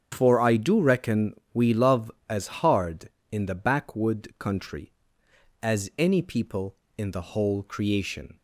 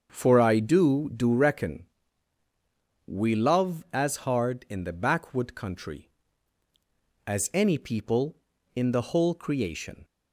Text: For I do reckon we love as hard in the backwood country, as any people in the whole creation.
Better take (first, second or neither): first